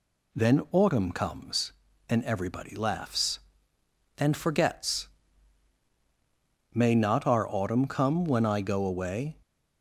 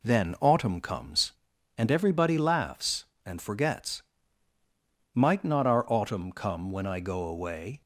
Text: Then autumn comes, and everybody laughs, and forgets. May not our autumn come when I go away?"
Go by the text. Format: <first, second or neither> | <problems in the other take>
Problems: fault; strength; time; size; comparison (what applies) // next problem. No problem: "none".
first | says "Might" for "May"; at 5.1 s